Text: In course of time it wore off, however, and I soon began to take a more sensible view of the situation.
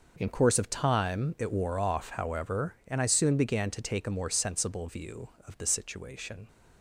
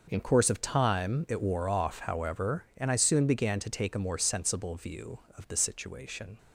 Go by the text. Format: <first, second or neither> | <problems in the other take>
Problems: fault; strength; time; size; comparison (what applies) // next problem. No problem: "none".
neither | none